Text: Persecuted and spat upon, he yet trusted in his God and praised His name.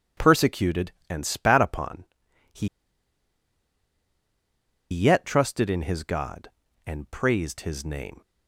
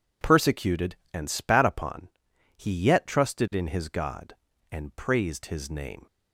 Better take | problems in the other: second | pauses between "he" and "yet"; strong; at 2.6 s; 2.2 s long

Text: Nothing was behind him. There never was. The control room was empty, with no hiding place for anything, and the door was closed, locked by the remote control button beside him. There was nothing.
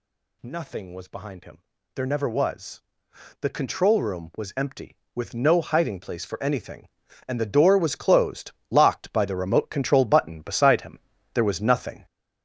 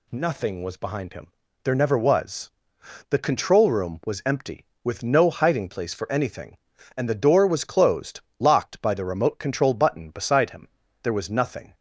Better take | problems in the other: second | gets louder; strong; throughout; 7.5 dB

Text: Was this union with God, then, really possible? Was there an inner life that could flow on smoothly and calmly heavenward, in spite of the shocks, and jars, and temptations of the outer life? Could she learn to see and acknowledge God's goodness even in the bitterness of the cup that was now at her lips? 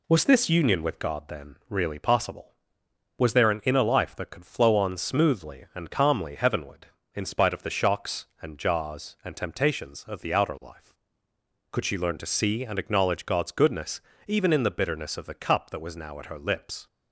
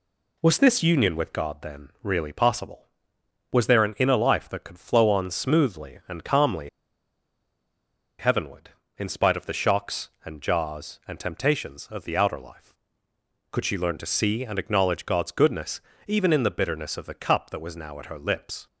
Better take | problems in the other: first | pauses between "calmly" and "heavenward"; strong; at 6.6 s; 1.5 s long // pauses between "goodness" and "even"; slight; at 15.7 s; 0.28 s long; slight in the first

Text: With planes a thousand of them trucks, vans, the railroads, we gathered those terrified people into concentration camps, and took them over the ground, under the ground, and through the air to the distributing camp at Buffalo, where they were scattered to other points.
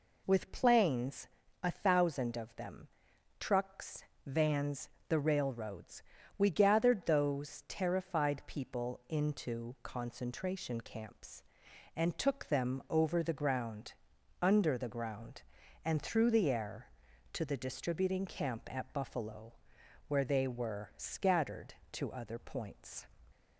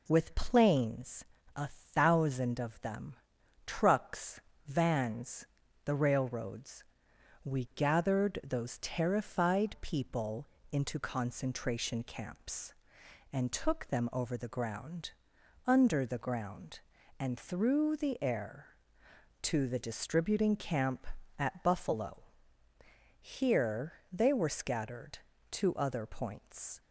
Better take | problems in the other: first | pauses between "planes" and "a"; slight; at 1.2 s; 0.32 s long; slight in the first // pauses between "them" and "trucks"; noticeable; at 3.1 s; 0.50 s long; noticeable in the first // pauses between "people" and "into"; slight; at 10.4 s; 0.24 s long // says "here" for "where"; at 23.1 s

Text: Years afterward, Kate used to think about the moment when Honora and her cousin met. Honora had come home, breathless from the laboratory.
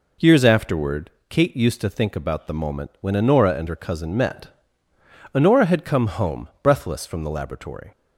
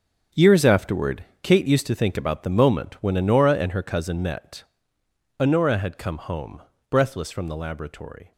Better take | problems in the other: first | gets quieter; strong; throughout; 12.5 dB

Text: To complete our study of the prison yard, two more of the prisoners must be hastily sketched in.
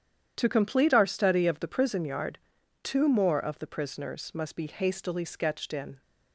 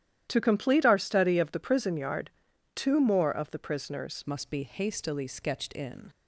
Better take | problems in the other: first | starts louder than the rest; strong; until 1.3 s; 11.5 dB; strong in the first // changes voice at "must"; from 4.2 s on; 1.8 s long

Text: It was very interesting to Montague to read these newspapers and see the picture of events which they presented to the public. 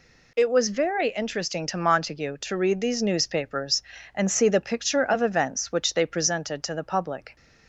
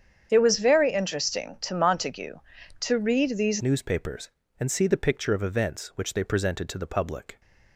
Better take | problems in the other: first | starts louder than the rest; strong; until 1.3 s; 8 dB // changes voice at "newspapers"; from 3.6 s on; 3.8 s long

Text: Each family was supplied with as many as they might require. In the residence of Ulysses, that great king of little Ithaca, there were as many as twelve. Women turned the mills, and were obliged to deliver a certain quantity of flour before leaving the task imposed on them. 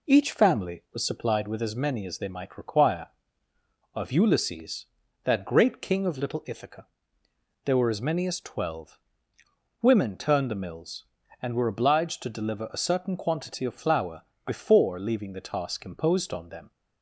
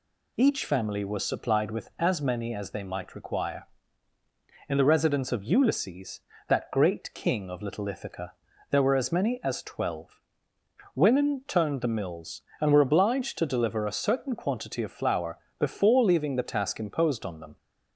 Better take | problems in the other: second | skips "In the residence"; at 3.5 s // pauses between "flour" and "before"; slight; at 14.2 s; 0.22 s long; slight in the second

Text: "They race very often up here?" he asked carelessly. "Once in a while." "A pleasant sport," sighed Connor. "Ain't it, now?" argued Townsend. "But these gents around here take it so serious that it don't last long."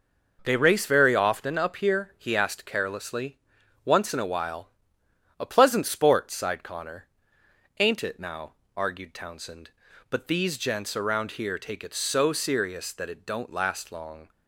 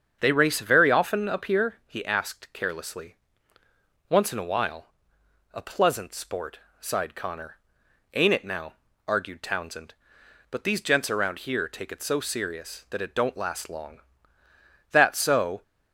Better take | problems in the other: first | starts louder than the rest; strong; until 1.2 s; 7.5 dB // goes on to say "That so"; noticeable; from 14.9 s on; 0.72 s long

